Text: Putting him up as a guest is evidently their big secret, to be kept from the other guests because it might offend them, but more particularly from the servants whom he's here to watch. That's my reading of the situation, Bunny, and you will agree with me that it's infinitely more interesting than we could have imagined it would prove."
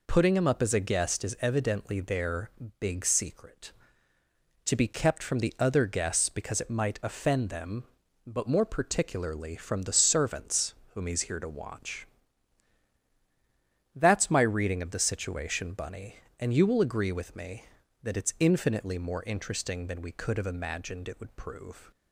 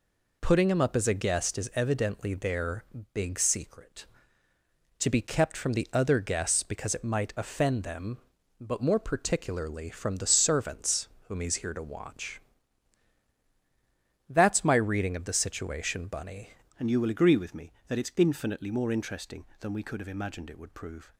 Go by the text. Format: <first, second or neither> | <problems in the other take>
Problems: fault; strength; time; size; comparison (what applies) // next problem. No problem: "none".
first | pauses between "their" and "big"; slight; at 2.8 s; 0.30 s long; slight in the first // pauses between "servants" and "whom"; slight; at 11.0 s; 0.20 s long; slight in the first // changes voice at "and"; from 16.7 s on; 4.4 s long